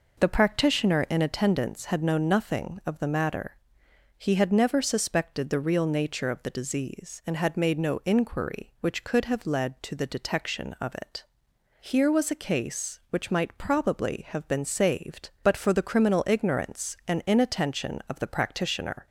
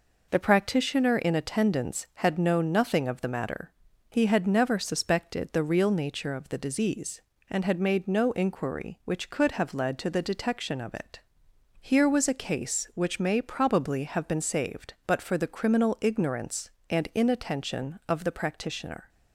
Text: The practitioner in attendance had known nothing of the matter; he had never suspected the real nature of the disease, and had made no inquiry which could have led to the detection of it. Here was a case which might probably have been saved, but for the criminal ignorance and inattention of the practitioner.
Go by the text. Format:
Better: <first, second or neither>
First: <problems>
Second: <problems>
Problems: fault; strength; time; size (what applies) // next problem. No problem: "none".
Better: first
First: none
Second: says "may" for "might"; at 13.2 s